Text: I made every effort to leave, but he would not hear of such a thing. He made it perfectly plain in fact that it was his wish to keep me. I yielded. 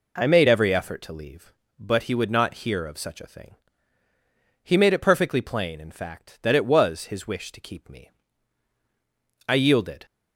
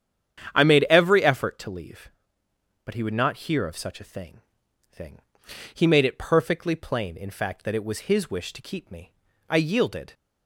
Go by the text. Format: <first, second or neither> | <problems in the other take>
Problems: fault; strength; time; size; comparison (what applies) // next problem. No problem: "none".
first | starts louder than the rest; strong; until 1.5 s; 9 dB // says "thing" twice; at 4.9 s